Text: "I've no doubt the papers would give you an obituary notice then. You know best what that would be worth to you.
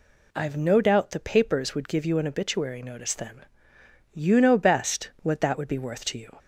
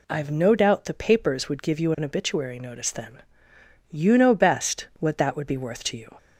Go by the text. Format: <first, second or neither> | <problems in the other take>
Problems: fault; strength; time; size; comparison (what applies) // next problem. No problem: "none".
neither | none